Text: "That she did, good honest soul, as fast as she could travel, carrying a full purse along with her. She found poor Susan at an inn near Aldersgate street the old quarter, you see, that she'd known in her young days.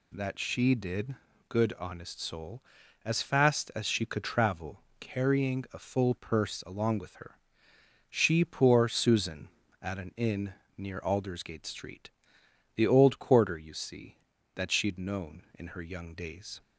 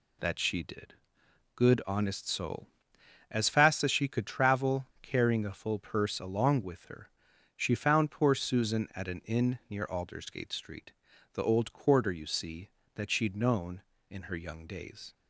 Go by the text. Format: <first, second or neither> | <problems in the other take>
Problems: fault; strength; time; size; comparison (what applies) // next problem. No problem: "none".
second | skips "found"; at 8.4 s // pauses between "inn" and "near"; slight; at 10.5 s; 0.24 s long // pauses between "street" and "the"; noticeable; at 12.0 s; 0.66 s long; also in the second